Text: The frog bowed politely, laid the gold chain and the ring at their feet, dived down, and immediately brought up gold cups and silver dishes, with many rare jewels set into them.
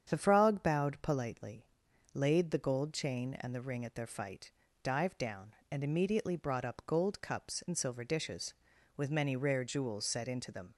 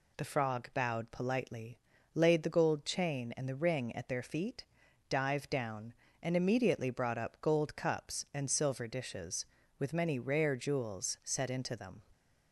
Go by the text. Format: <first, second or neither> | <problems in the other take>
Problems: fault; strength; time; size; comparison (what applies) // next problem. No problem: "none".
second | starts louder than the rest; strong; until 1.0 s; 8 dB // says "fight" for "feet"; at 4.0 s